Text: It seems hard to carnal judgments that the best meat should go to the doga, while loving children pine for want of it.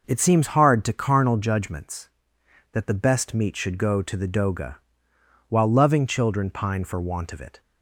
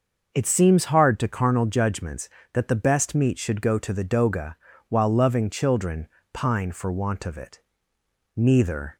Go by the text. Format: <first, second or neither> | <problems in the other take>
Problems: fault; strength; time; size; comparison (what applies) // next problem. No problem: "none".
first | starts louder than the rest; noticeable; until 1.3 s; 6 dB // pauses between "children" and "pine"; slight; at 6.0 s; 0.24 s long // goes on to say "Neither"; noticeable; from 8.3 s on; 0.62 s long